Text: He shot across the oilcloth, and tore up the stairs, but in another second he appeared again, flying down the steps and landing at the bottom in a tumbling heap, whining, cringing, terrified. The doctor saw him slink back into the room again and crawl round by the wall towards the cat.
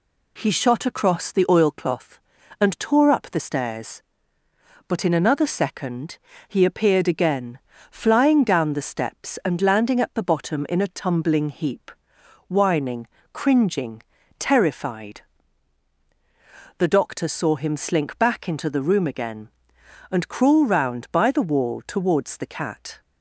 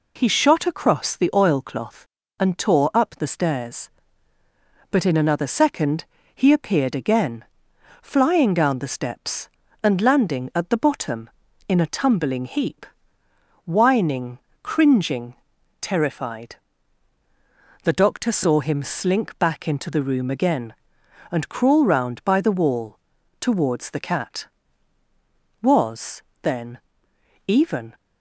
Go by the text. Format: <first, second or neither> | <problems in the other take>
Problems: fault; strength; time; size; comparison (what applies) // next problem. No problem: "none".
first | pauses between "second" and "he"; slight; at 6.0 s; 0.28 s long; slight in the first // pauses between "wall" and "towards"; at 22.9 s; 0.42 s long // goes on to say "Was then even"; strong; from 25.6 s on; 2.3 s long